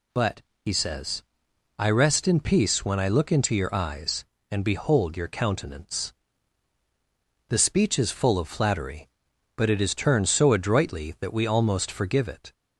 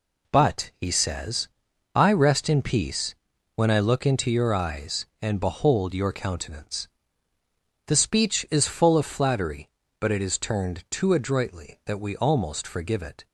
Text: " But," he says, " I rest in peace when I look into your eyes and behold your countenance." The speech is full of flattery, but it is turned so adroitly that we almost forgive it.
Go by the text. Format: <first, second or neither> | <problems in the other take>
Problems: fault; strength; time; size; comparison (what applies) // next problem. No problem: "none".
first | pauses between "peace" and "when"; at 3.1 s; 0.40 s long // says "too" for "so"; at 10.8 s